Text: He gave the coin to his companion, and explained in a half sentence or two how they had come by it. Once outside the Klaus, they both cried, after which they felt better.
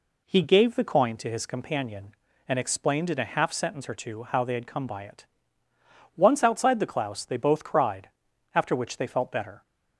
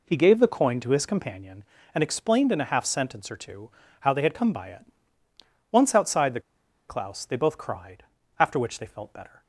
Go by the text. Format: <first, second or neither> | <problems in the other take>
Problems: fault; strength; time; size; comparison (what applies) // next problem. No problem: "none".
first | pauses between "two" and "how"; slight; at 3.7 s; 0.30 s long // pauses between "the" and "Klaus"; noticeable; at 6.3 s; 0.49 s long